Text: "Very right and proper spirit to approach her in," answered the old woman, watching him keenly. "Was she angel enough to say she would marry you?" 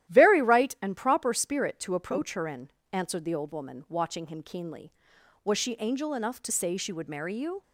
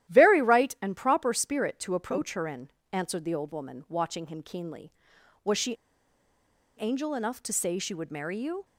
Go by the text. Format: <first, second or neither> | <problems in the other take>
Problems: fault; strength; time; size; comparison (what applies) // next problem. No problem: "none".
first | starts louder than the rest; strong; until 1.1 s; 13 dB; strong in the first // pauses between "she" and "angel"; at 5.7 s; 1.0 s long